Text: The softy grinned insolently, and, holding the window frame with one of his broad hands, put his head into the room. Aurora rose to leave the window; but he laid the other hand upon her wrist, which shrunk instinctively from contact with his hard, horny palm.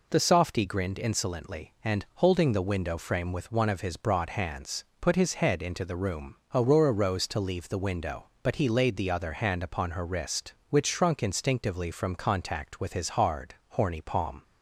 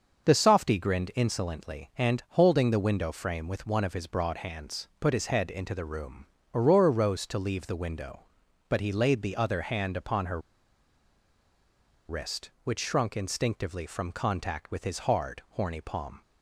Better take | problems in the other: first | starts louder than the rest; until 1.3 s; 6.5 dB // pauses between "her" and "wrist"; strong; at 10.4 s; 1.6 s long

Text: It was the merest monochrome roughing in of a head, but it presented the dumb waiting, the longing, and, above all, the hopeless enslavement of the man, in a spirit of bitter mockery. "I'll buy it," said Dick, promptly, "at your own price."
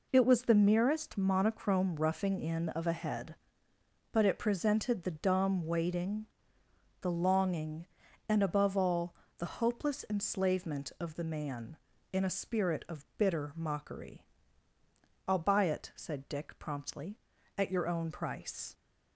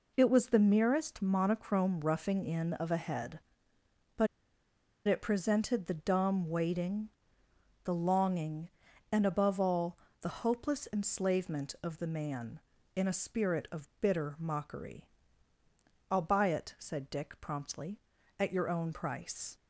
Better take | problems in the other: first | pauses between "but" and "it"; noticeable; at 4.2 s; 0.80 s long

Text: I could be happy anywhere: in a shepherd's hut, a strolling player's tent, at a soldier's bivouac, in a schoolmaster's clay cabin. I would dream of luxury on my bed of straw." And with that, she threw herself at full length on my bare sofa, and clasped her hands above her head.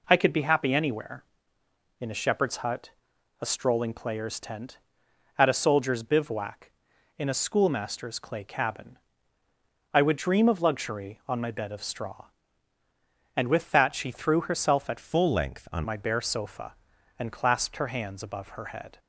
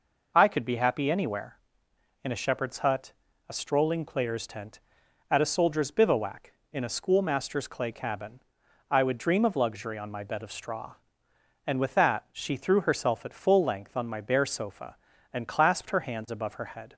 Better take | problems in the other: second | changes voice from "full" to "on"; from 14.9 to 15.8 s; 0.9 s long

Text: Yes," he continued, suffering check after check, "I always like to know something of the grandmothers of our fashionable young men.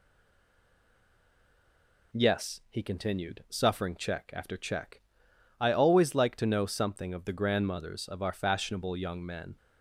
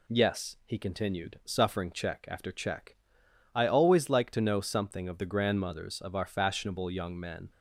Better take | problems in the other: second | stays silent before the first word; until 2.1 s; 2.1 s long

